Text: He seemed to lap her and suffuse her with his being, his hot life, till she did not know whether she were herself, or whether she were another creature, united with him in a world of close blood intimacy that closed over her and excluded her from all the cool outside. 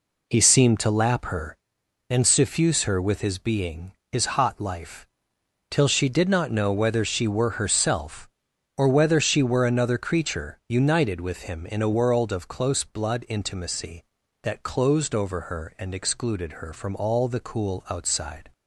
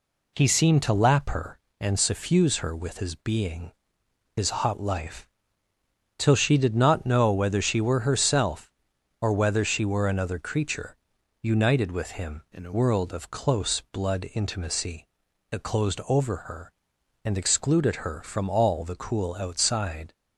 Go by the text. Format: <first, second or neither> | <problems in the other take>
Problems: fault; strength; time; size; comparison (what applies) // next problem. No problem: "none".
first | changes voice from "in" to "a"; from 12.5 to 12.7 s; 0.2 s long